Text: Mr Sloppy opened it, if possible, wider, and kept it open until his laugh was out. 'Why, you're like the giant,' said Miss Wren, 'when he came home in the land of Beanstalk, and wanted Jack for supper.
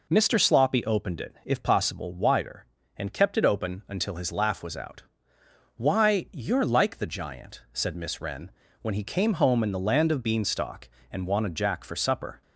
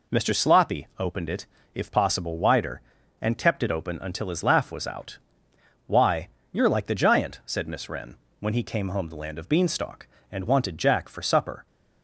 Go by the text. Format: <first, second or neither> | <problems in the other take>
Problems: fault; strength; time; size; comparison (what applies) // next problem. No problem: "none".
first | skips "in"; at 9.0 s